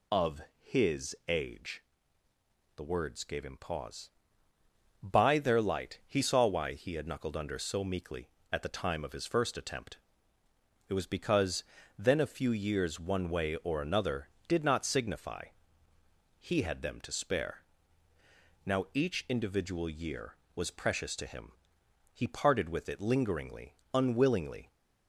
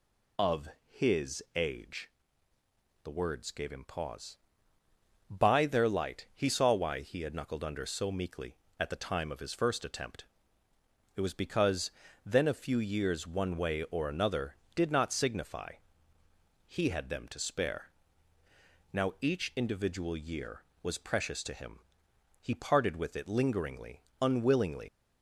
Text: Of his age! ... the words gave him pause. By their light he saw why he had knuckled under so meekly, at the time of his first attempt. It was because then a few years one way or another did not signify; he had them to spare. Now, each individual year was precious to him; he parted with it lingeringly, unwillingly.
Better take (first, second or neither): first